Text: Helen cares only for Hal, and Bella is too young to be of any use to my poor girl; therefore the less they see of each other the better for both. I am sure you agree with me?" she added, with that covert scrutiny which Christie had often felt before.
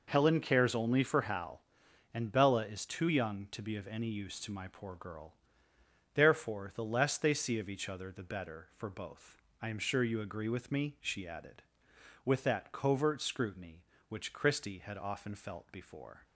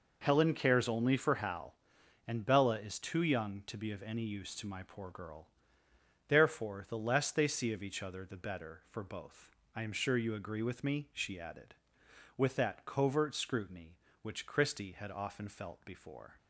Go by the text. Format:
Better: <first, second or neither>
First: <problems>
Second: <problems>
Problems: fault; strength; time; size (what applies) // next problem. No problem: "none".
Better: neither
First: none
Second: none